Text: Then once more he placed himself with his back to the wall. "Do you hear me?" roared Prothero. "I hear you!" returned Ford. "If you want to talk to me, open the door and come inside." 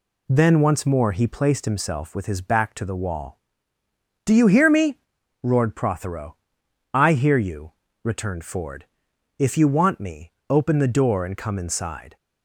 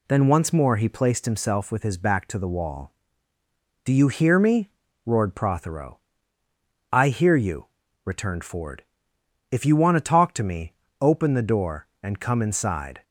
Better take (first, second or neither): second